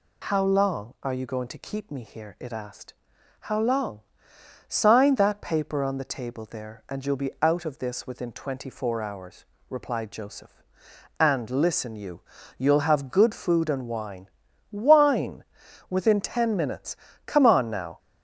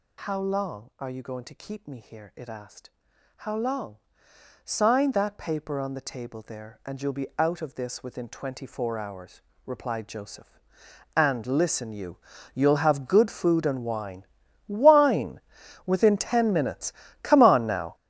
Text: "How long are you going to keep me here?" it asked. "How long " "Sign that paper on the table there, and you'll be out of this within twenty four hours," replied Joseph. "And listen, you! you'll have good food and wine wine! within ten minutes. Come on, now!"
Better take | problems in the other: first | gets louder; strong; throughout; 14 dB // pauses between "wine" and "wine"; at 14.2 s; 0.42 s long; also in the first

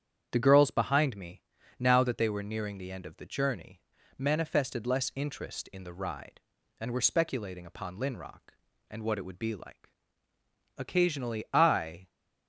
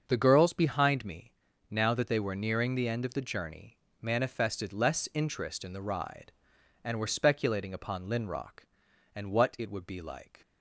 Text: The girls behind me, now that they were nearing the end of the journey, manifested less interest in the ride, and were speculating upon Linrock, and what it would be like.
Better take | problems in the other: second | starts louder than the rest; strong; until 1.3 s; 8.5 dB; also in the second // goes on to say "Occasionally I"; noticeable; from 10.7 s on; 1.3 s long

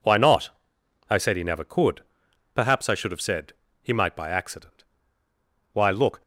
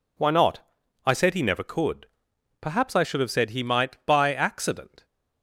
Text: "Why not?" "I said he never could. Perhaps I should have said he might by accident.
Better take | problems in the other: second | pauses between "said" and "he"; slight; at 3.5 s; 0.30 s long // goes on to say "Why look"; slight; from 5.7 s on; 0.48 s long

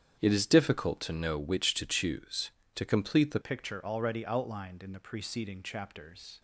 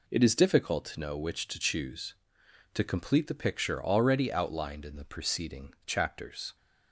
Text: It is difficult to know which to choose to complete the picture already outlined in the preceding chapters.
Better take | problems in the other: second | starts louder than the rest; strong; until 1.2 s; 8.5 dB // changes voice at "picture"; from 3.4 s on; 3.0 s long

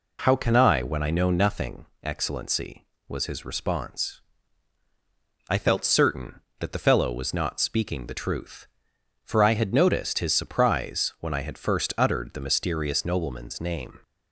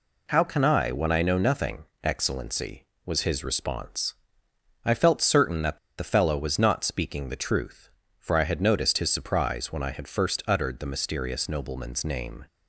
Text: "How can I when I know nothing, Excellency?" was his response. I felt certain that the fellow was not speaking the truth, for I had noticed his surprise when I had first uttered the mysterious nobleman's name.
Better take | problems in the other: first | pauses between "that" and "the"; slight; at 5.7 s; 0.20 s long

